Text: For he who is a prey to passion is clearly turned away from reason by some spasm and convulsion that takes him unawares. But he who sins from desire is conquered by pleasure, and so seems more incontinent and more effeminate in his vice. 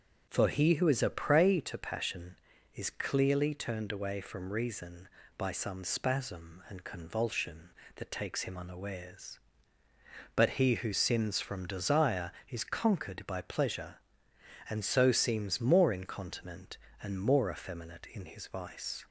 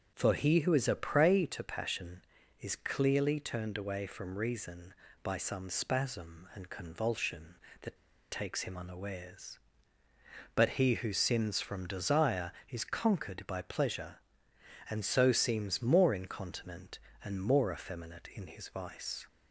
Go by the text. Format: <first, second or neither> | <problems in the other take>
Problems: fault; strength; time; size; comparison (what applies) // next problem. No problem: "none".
first | starts louder than the rest; until 1.1 s; 7 dB; also in the first // pauses between "that" and "takes"; slight; at 7.9 s; 0.34 s long